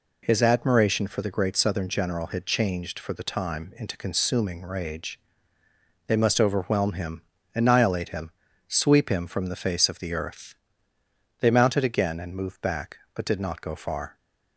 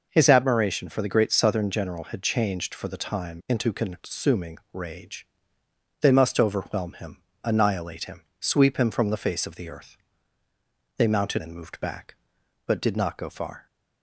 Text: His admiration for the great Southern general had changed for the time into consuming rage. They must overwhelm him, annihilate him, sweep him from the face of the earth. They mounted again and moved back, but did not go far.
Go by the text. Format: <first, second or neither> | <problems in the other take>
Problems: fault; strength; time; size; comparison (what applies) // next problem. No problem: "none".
first | pauses between "consuming" and "rage"; slight; at 4.5 s; 0.16 s long // skips "again"; at 11.4 s